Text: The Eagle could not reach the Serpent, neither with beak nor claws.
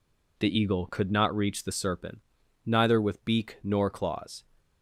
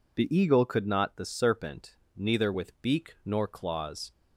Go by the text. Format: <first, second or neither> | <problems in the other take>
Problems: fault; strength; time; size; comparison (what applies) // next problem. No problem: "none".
first | skips "reach"; at 1.1 s